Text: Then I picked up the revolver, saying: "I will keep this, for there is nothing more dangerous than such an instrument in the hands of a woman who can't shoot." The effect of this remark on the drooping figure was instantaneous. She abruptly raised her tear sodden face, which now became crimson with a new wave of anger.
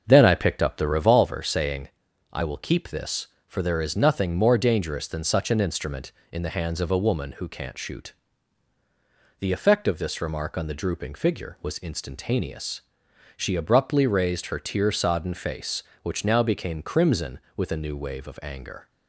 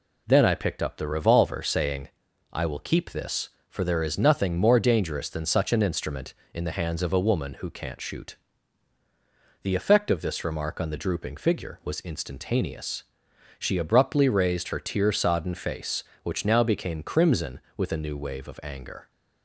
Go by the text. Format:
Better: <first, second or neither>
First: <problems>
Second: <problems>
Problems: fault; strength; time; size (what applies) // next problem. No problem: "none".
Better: second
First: starts louder than the rest; until 1.2 s; 6.5 dB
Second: none